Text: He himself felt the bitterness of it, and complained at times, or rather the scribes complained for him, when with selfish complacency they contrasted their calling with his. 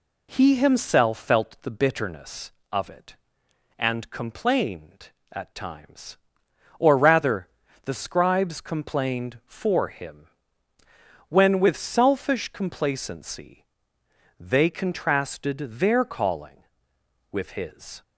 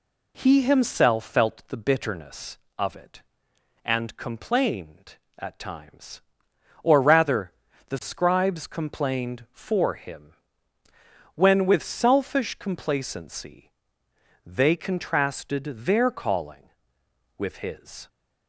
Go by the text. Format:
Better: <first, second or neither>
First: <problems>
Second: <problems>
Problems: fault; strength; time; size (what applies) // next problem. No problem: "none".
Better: neither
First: pauses between "rather" and "the"; slight; at 7.4 s; 0.34 s long // pauses between "complacency" and "they"; noticeable; at 13.6 s; 0.74 s long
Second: pauses between "rather" and "the"; slight; at 7.5 s; 0.34 s long // pauses between "complacency" and "they"; noticeable; at 13.7 s; 0.74 s long